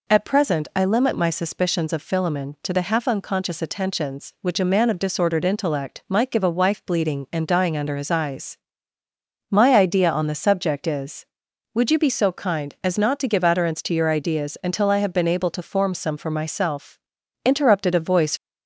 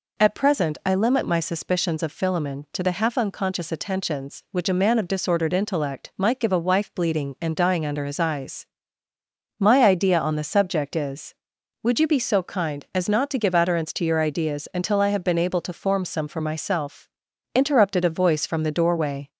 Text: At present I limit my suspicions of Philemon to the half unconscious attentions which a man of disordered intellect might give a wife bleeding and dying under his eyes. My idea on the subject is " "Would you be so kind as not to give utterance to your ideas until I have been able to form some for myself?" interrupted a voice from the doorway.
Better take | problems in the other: second | stops before "from the doorway"; at 18.3 s

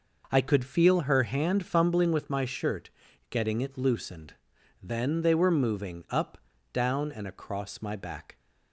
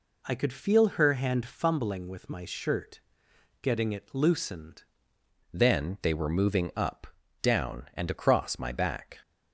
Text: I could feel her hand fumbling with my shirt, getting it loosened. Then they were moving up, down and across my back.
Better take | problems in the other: first | changes voice at "Then"; from 5.5 s on; 3.6 s long

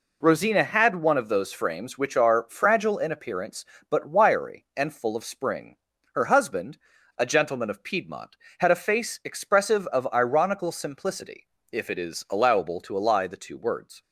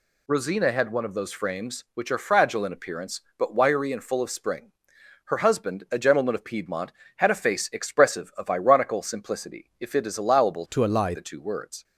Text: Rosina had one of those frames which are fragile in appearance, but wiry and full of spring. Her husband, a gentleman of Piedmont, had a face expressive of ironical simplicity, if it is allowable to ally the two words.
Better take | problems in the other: first | changes voice from "to" to "ally"; from 10.7 to 11.1 s; 0.4 s long

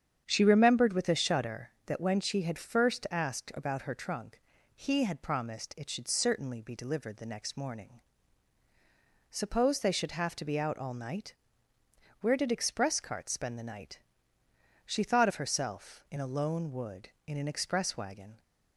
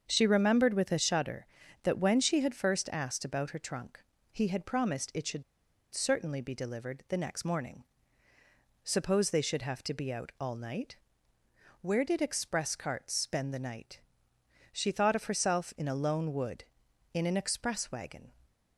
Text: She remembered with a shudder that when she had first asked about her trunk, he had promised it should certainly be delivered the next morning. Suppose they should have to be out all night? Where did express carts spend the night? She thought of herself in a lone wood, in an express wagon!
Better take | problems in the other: first | starts louder than the rest; until 1.0 s; 7 dB; strong in the first // pauses between "should" and "certainly"; noticeable; at 5.4 s; 0.50 s long

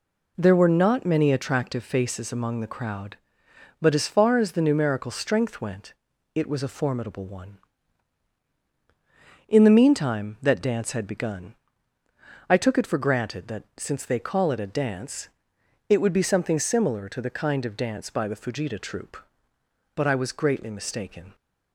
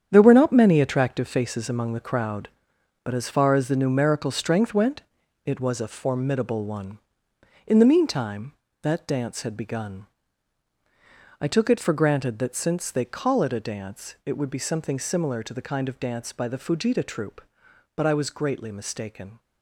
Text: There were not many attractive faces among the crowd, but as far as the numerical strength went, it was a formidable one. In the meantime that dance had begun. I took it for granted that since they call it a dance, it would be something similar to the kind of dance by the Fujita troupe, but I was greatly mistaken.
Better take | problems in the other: first | gets quieter; strong; throughout; 9.5 dB

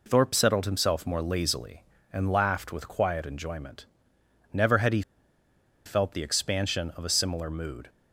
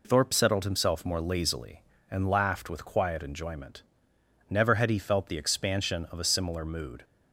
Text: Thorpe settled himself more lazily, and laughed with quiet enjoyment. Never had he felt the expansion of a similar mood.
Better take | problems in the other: second | pauses between "he" and "felt"; noticeable; at 5.0 s; 0.84 s long

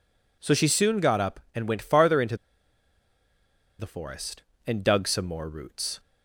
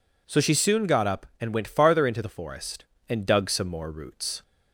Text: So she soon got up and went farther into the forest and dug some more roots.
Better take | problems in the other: second | pauses between "into" and "the"; strong; at 2.3 s; 1.4 s long

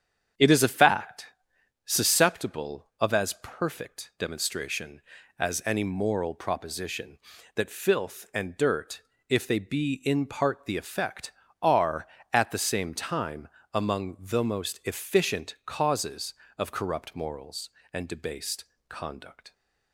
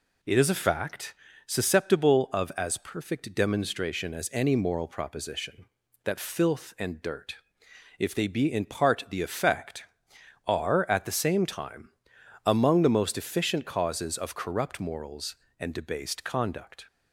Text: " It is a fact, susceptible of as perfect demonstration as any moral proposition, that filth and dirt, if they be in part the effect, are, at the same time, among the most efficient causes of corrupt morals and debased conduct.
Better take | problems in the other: second | starts louder than the rest; strong; until 1.3 s; 8 dB // pauses between "debased" and "conduct"; slight; at 18.6 s; 0.24 s long

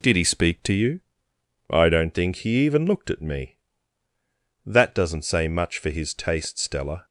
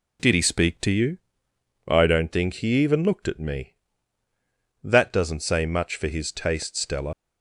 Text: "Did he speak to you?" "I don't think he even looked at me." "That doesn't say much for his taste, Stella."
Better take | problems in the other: first | leaves "Stella" unfinished; at 7.1 s; 95 ms

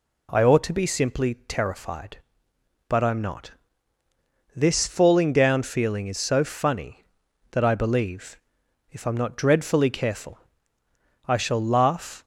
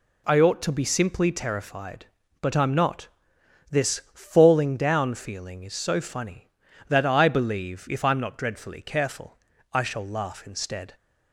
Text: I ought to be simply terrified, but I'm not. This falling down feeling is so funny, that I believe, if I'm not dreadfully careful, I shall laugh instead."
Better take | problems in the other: second | stops before "instead"; at 12.2 s

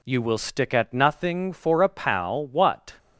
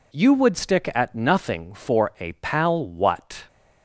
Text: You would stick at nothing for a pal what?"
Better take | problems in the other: second | says "will" for "would"; at 0.1 s

